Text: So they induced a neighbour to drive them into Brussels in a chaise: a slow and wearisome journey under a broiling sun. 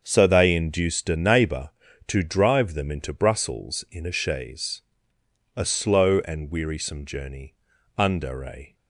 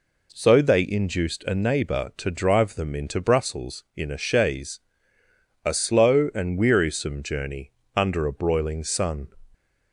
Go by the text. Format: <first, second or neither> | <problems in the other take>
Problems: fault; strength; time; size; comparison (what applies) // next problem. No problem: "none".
second | starts louder than the rest; until 1.0 s; 6.5 dB // pauses between "journey" and "under"; at 7.5 s; 0.42 s long; slight in the second // stops before "broiling sun"; at 8.7 s